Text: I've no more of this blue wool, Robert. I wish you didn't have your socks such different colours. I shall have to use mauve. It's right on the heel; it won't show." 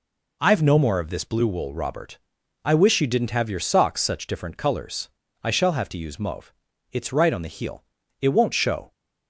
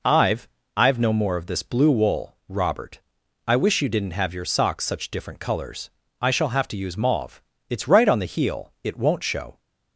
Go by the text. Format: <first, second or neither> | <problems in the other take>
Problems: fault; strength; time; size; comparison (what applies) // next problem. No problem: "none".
first | says "I've" twice; at 0.7 s